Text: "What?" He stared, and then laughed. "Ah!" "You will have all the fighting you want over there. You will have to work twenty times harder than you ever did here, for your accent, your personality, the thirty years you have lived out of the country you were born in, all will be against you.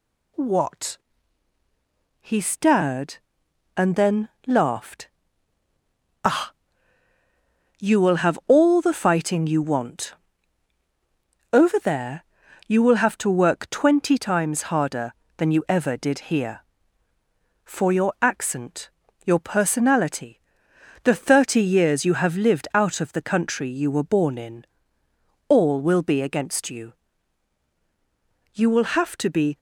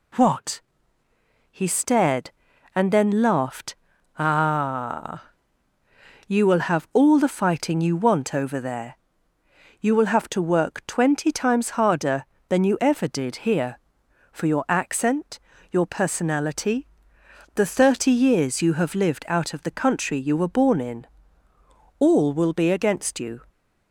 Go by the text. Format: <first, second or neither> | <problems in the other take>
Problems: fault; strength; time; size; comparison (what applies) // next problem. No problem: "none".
second | pauses between "then" and "laughed"; slight; at 4.2 s; 0.16 s long // pauses between "want" and "over"; strong; at 10.1 s; 1.3 s long // goes on to say "You will have to be"; noticeable; from 28.5 s on; 1.0 s long